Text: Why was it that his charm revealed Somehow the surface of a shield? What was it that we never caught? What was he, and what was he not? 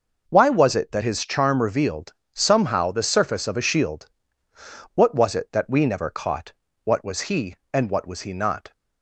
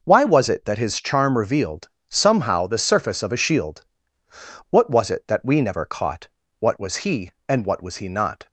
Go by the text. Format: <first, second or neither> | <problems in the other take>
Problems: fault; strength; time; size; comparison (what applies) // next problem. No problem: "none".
neither | pauses between "revealed" and "Somehow"; slight; the same in both